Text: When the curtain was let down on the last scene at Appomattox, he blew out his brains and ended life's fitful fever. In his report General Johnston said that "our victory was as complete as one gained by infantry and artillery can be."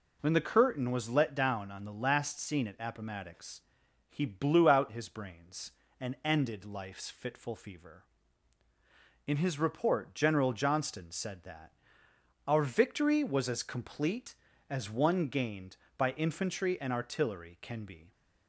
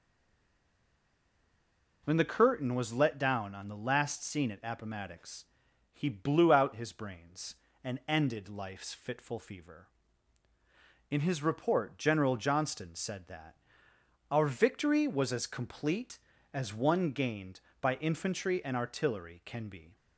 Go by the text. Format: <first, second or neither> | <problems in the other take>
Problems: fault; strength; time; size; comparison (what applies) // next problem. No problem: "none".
first | stays silent before the first word; noticeable; until 2.0 s; 2.0 s long // pauses between "that" and "our"; noticeable; at 13.5 s; 0.74 s long; noticeable in the first